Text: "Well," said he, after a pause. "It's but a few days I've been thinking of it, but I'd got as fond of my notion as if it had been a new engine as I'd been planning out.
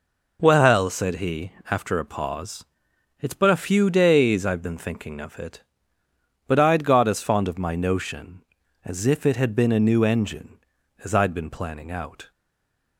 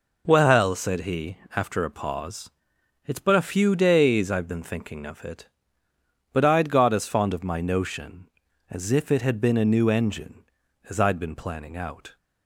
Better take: second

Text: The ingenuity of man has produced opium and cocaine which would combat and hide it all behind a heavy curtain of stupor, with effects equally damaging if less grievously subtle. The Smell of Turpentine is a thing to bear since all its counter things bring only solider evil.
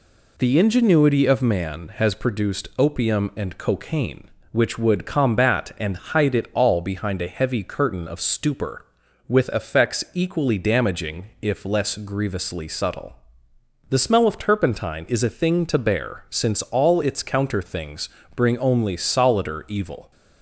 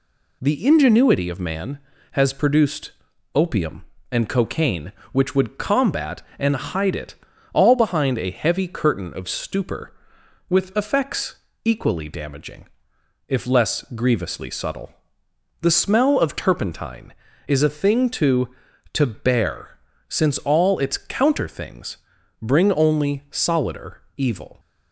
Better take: first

